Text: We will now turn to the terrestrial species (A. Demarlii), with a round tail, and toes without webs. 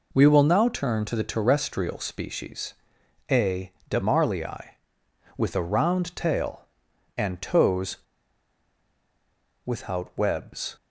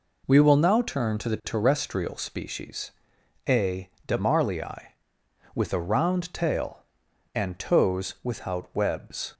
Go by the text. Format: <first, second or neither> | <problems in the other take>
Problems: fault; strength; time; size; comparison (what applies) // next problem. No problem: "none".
second | pauses between "toes" and "without"; strong; at 7.9 s; 1.6 s long